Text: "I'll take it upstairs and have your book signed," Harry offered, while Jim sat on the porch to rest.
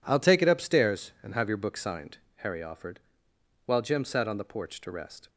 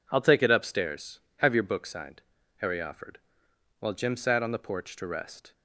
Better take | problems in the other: first | skips "and"; at 1.2 s

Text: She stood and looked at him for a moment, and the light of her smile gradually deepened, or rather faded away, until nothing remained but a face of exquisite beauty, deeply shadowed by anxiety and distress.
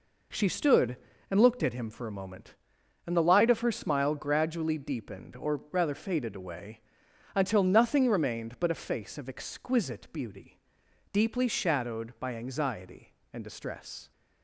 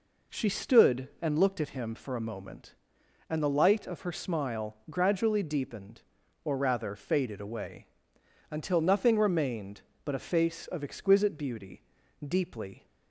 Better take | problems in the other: first | stops before "shadowed by anxiety and distress"; at 12.8 s

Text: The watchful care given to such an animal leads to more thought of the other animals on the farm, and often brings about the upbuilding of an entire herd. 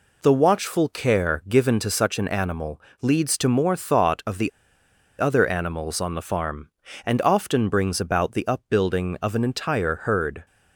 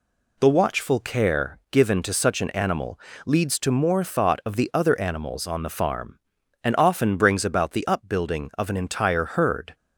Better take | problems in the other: second | pauses between "animal" and "leads"; slight; at 2.8 s; 0.20 s long; slight in the second // pauses between "the" and "other"; noticeable; at 4.4 s; 0.69 s long

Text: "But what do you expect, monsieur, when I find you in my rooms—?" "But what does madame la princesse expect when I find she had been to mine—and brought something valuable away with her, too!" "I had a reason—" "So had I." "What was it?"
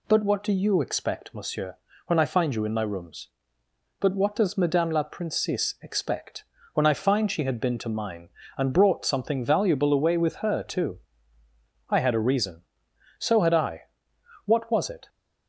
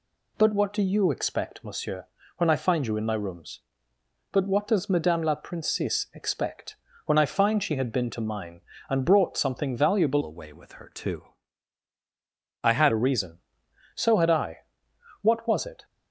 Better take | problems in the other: first | pauses between "expect" and "when"; slight; at 6.7 s; 0.32 s long; slight in the first // changes voice from "away" to "had"; from 10.2 to 12.9 s; 2.7 s long

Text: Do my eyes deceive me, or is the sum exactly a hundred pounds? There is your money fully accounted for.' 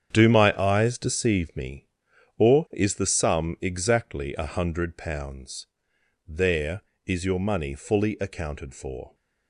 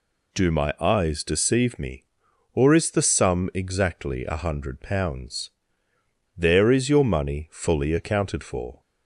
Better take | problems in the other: second | gets quieter; strong; throughout; 10.5 dB

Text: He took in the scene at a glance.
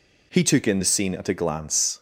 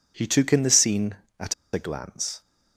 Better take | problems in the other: first | pauses between "at" and "a"; slight; at 1.5 s; 0.20 s long

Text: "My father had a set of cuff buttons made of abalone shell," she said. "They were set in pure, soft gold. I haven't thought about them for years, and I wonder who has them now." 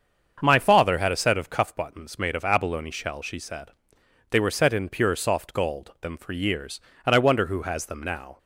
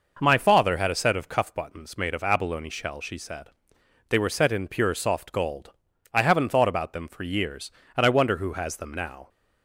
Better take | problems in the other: second | starts louder than the rest; until 1.4 s; 7 dB // skips "I haven't thought about"; at 5.9 s

